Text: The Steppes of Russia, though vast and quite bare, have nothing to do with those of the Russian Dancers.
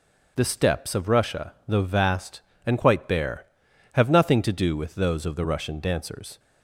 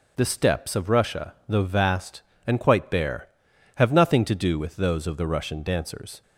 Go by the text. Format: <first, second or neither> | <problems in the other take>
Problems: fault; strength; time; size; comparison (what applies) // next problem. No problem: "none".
neither | none